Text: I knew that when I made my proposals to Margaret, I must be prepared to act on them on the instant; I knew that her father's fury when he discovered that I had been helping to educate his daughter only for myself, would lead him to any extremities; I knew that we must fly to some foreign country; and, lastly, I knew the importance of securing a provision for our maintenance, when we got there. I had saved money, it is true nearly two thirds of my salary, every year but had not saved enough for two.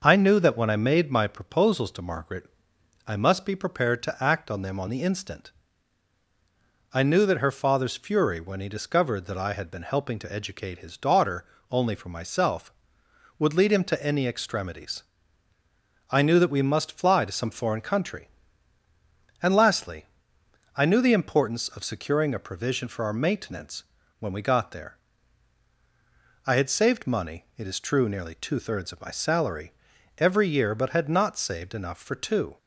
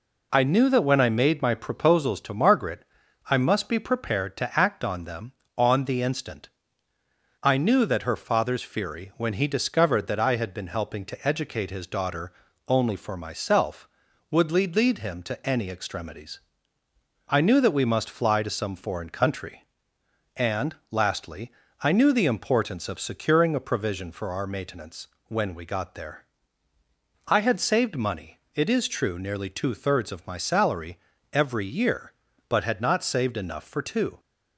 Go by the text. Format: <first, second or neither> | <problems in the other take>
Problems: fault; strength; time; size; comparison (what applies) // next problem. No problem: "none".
first | pauses between "daughter" and "only"; slight; at 12.3 s; 0.36 s long; slight in the first // says "lead" twice; at 14.7 s